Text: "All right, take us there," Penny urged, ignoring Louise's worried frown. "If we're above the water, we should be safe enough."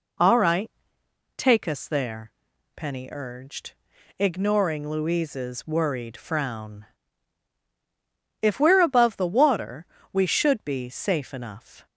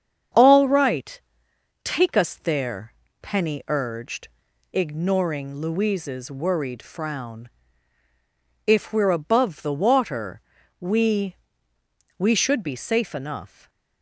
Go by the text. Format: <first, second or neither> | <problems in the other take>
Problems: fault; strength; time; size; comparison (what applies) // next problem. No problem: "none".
first | starts louder than the rest; strong; until 1.9 s; 7.5 dB // says "we" twice; at 12.1 s // stays silent after the last word; slight; from 13.4 s on; 0.6 s long